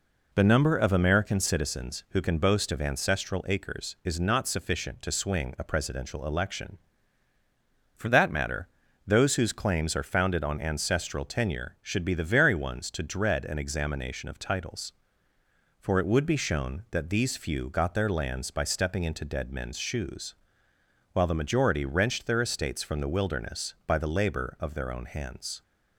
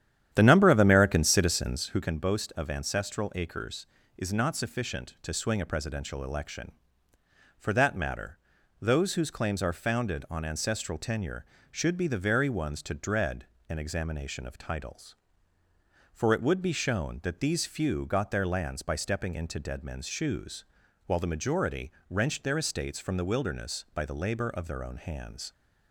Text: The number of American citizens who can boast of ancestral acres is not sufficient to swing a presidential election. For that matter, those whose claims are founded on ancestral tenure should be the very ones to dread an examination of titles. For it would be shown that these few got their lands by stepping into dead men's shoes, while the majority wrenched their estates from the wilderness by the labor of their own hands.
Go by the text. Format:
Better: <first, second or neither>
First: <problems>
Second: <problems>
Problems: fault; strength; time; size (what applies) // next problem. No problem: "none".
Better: first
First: none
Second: starts louder than the rest; strong; until 2.1 s; 10 dB // pauses between "dread" and "an"; slight; at 13.4 s; 0.24 s long // pauses between "majority" and "wrenched"; slight; at 21.9 s; 0.16 s long